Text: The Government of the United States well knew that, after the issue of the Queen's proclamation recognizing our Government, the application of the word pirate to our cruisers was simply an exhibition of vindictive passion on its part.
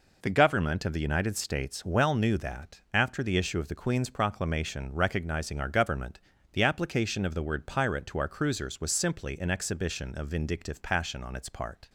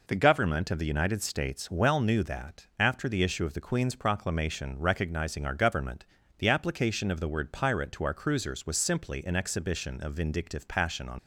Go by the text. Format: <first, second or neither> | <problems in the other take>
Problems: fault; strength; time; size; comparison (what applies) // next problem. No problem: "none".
first | stops before "its part"; at 11.1 s